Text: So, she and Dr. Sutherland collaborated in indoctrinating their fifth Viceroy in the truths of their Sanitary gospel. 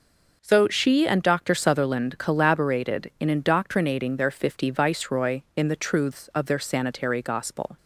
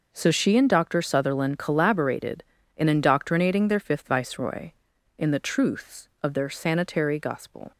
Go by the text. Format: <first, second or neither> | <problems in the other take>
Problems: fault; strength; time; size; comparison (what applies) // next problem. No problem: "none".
second | says "fifty" for "fifth"; at 4.2 s